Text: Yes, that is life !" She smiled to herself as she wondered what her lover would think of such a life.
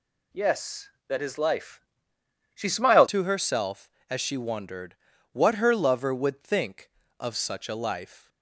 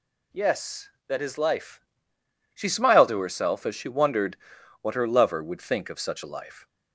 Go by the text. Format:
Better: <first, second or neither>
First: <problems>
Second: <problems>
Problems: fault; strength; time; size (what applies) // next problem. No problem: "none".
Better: second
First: changes voice at "to"; from 3.0 s on; 5.2 s long // pauses between "wondered" and "what"; at 4.9 s; 0.38 s long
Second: pauses between "wondered" and "what"; at 4.3 s; 0.44 s long